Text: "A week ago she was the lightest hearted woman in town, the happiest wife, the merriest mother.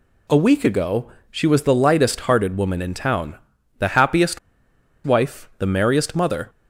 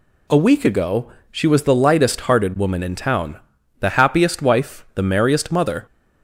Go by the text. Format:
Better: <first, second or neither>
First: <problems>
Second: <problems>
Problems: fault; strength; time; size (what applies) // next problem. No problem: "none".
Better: second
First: pauses between "ago" and "she"; slight; at 1.1 s; 0.20 s long // pauses between "happiest" and "wife"; noticeable; at 4.3 s; 0.65 s long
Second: pauses between "ago" and "she"; slight; at 1.1 s; 0.20 s long